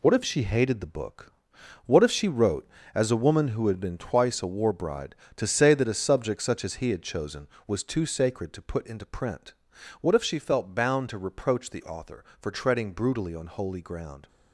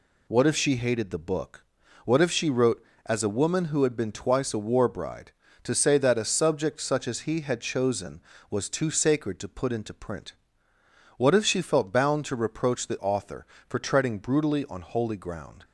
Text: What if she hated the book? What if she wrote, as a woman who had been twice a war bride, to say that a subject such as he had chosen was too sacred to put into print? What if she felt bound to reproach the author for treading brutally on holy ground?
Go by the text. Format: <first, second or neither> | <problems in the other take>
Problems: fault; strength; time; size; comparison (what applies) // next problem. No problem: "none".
neither | none